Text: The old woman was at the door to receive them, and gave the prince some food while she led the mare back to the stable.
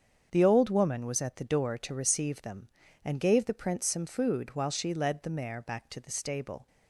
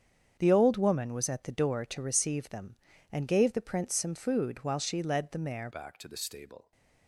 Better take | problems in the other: first | starts louder than the rest; strong; until 1.4 s; 8 dB; strong in the first // changes voice at "back"; from 5.7 s on; 1.0 s long

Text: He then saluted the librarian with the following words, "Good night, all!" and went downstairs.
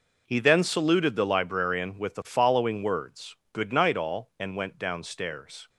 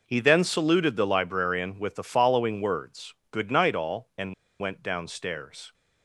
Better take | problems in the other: first | pauses between "and" and "went"; slight; at 4.3 s; 0.27 s long

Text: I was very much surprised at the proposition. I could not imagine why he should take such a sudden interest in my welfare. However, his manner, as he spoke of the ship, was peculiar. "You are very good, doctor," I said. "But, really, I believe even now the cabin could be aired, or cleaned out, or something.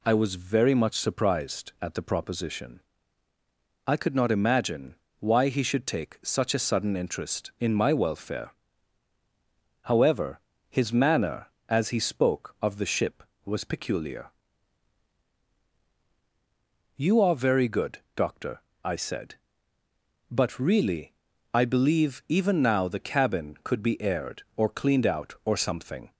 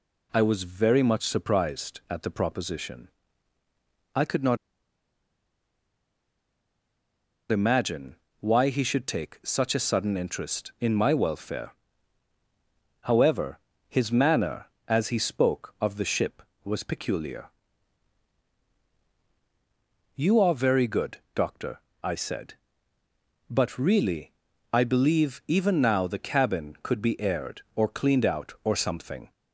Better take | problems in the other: first | pauses between "not" and "imagine"; strong; at 4.5 s; 2.9 s long // pauses between "imagine" and "why"; slight; at 8.1 s; 0.24 s long; slight in the first

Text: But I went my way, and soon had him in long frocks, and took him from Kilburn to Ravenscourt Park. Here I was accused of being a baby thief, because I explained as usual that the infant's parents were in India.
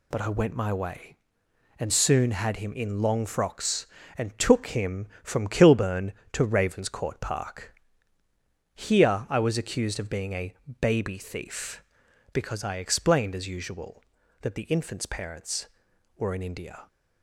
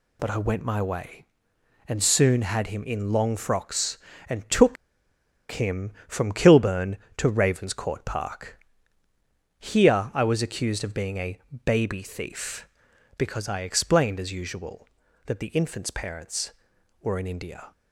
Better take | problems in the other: first | pauses between "took" and "him"; noticeable; at 4.7 s; 0.75 s long // pauses between "a" and "baby"; slight; at 11.3 s; 0.28 s long; slight in the first

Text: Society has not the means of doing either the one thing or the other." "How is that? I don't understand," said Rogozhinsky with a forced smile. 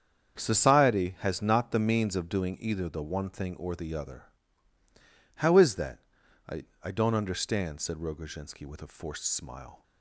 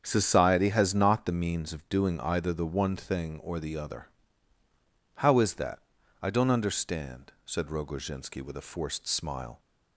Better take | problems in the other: second | starts louder than the rest; strong; until 1.4 s; 7.5 dB; strong in the second // says "I" twice; at 6.8 s

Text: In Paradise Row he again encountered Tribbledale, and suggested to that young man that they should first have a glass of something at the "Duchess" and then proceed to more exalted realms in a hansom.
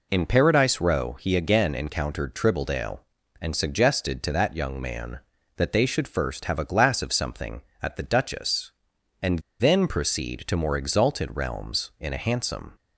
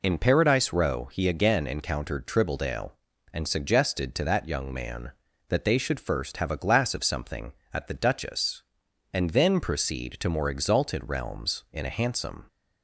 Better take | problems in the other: second | pauses between "and" and "then"; slight; at 9.3 s; 0.21 s long

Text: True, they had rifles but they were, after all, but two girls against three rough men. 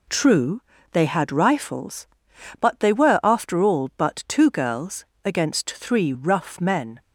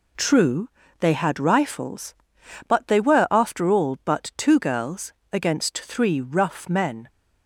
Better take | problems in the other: neither | pauses between "girls" and "against"; slight; the same in both

